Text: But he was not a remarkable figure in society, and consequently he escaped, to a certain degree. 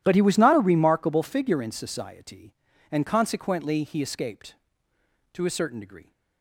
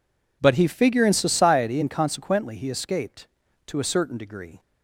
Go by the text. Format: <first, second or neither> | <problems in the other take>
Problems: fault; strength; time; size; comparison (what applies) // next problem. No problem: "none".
first | skips "was not a remarkable"; at 0.6 s